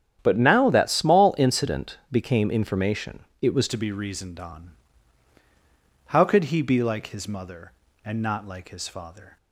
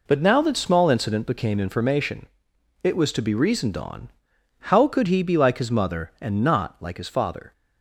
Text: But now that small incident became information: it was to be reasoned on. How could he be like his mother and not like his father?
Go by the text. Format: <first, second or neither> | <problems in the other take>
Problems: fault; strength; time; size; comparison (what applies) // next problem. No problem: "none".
second | starts louder than the rest; strong; until 1.2 s; 9.5 dB // changes voice at "to"; from 3.6 s on; 5.7 s long